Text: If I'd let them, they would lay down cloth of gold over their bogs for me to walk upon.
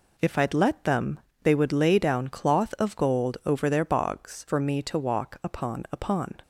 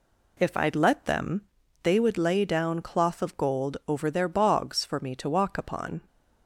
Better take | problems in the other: second | says "upon" twice; at 5.9 s

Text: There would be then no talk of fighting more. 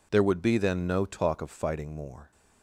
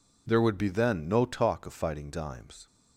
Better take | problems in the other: first | says "dimes" for "more"; at 2.1 s

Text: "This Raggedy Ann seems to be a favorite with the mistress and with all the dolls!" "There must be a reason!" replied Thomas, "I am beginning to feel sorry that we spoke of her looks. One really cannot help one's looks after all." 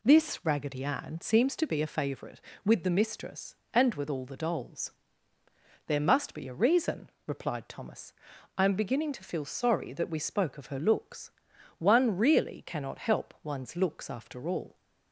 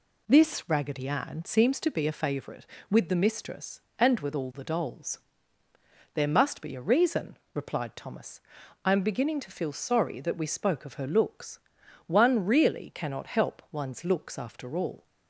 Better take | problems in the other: neither | none

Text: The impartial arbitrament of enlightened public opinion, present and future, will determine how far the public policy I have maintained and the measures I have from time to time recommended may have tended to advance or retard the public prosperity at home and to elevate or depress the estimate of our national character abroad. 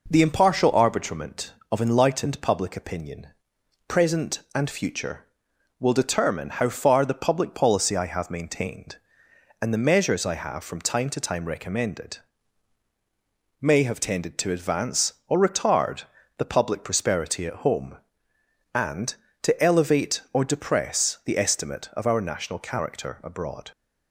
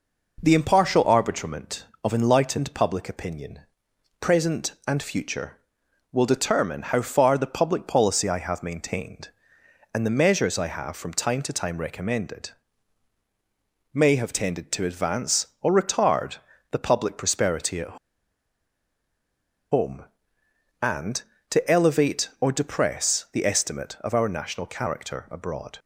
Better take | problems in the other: first | pauses between "recommended" and "may"; strong; at 12.5 s; 1.4 s long; strong in the first // pauses between "retard" and "the"; slight; at 16.3 s; 0.34 s long; slight in the first // pauses between "at" and "home"; strong; at 17.9 s; 1.7 s long

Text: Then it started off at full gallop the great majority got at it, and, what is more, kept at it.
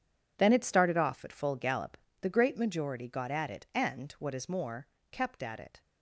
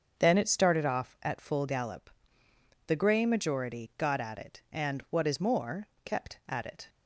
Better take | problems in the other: first | starts louder than the rest; until 1.2 s; 6.5 dB // pauses between "gallop" and "the"; noticeable; at 2.1 s; 0.76 s long; slight in the first // says "grey" for "great"; at 2.9 s

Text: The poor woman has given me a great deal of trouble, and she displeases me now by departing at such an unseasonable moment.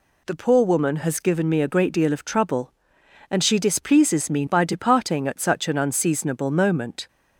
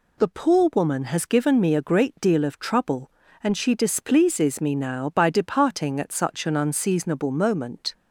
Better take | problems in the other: second | skips "now"; at 4.4 s

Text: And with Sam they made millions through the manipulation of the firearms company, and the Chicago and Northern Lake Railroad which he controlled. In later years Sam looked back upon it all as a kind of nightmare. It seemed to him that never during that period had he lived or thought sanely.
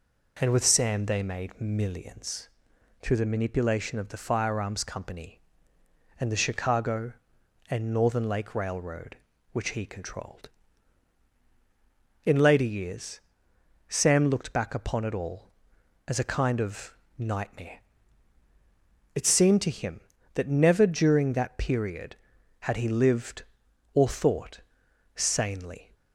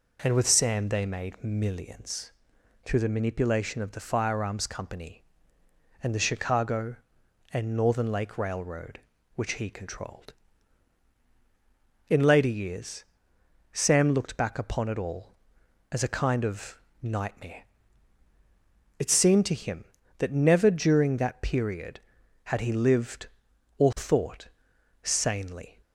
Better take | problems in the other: neither | pauses between "millions" and "through"; noticeable; the same in both // pauses between "years" and "Sam"; noticeable; the same in both // pauses between "of" and "nightmare"; slight; the same in both // pauses between "thought" and "sanely"; noticeable; the same in both

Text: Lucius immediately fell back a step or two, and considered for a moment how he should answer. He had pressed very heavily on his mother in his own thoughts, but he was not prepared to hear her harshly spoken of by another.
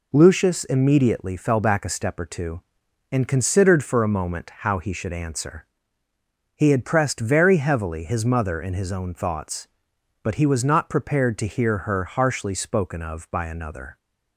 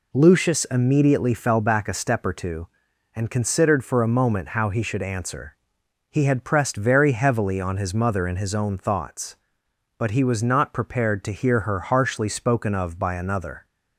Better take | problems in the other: second | skips "on"; at 8.0 s

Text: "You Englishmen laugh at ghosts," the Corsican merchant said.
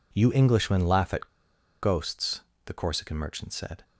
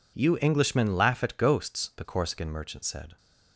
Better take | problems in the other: second | pauses between "at" and "ghosts"; noticeable; at 1.2 s; 0.52 s long

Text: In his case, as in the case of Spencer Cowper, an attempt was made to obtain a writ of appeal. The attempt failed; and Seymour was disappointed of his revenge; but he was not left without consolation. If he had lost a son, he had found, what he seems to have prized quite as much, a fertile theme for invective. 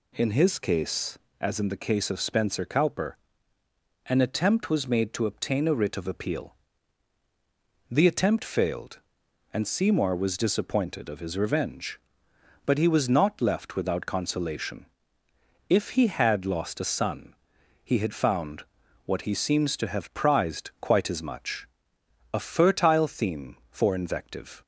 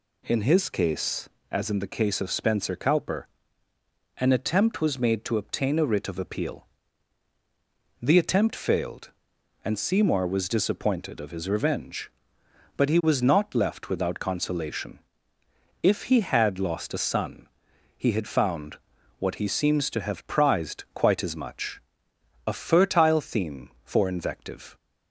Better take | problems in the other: neither | none

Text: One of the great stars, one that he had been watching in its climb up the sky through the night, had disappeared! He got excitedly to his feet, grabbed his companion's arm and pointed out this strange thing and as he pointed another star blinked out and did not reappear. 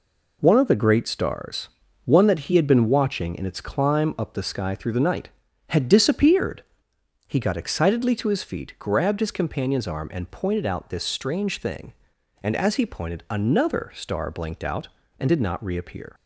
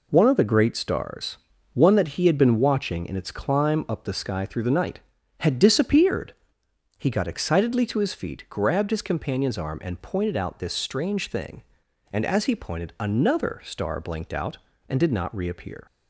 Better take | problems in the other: neither | none

